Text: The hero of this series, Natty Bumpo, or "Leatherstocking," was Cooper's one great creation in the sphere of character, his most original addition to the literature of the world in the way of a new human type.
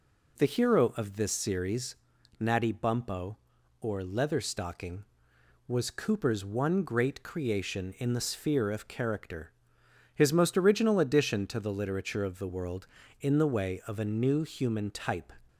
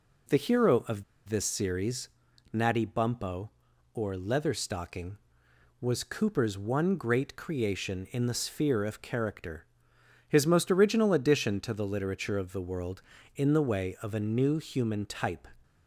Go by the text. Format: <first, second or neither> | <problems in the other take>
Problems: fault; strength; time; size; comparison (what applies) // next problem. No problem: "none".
first | pauses between "of" and "this"; slight; at 1.0 s; 0.24 s long